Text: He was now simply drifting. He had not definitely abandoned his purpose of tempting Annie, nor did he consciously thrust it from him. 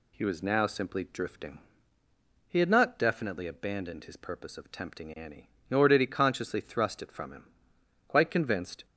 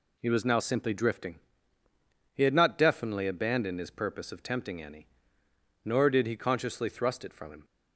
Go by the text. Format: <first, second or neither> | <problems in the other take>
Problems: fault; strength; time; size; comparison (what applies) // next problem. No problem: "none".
second | goes on to say "Quite convinced"; noticeable; from 8.0 s on; 0.76 s long